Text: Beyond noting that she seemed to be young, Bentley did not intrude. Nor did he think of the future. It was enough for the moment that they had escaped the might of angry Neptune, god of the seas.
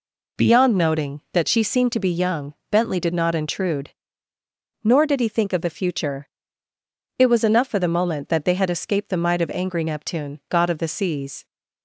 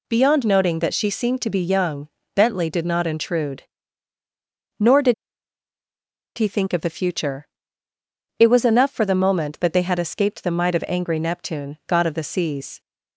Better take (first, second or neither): first